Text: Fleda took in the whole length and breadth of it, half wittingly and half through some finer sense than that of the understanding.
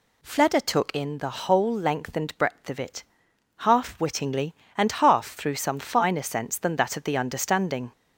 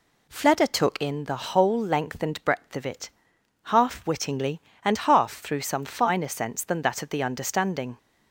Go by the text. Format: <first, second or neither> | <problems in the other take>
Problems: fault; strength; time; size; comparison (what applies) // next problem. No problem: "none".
second | gets louder; slight; throughout; 2.5 dB